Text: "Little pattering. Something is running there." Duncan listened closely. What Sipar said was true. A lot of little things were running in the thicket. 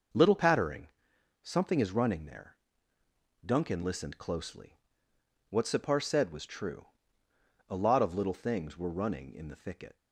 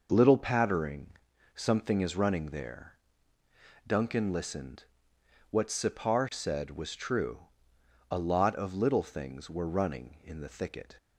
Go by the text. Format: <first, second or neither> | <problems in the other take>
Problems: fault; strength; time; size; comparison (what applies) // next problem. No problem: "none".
first | skips "closely"; at 5.1 s